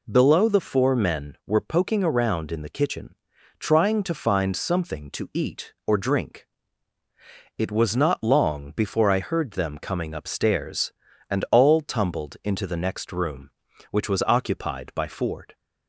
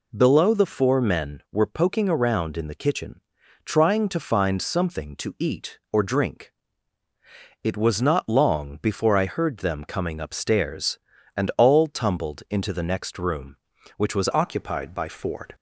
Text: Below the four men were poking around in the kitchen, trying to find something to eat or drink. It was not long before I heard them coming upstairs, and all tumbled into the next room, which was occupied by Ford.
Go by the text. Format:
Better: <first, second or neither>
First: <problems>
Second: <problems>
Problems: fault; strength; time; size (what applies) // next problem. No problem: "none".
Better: first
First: none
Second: changes voice at "occupied"; from 14.3 s on; 1.2 s long